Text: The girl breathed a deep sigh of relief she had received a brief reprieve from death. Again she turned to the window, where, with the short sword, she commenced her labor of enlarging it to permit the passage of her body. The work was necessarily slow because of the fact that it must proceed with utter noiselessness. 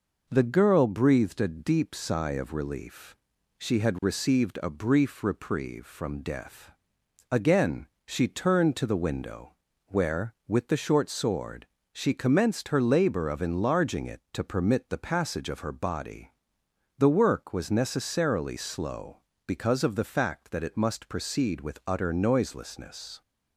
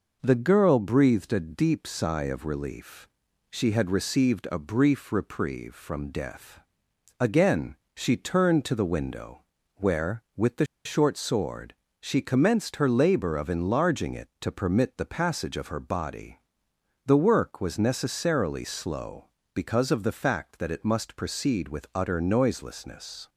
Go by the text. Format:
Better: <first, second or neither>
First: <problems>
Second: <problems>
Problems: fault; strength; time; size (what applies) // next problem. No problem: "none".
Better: first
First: pauses between "relief" and "she"; at 3.1 s; 0.42 s long // pauses between "Again" and "she"; slight; at 7.8 s; 0.20 s long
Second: pauses between "relief" and "she"; at 3.0 s; 0.42 s long // pauses between "Again" and "she"; slight; at 7.7 s; 0.20 s long // pauses between "the" and "short"; slight; at 10.6 s; 0.19 s long